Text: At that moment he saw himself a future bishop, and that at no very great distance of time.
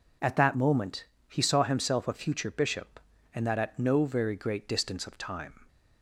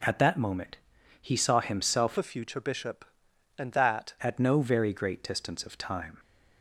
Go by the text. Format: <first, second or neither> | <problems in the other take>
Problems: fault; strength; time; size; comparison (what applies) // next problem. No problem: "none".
first | pauses between "moment" and "he"; at 0.7 s; 0.42 s long; slight in the first // changes voice from "a" to "that"; from 2.1 to 4.1 s; 2.0 s long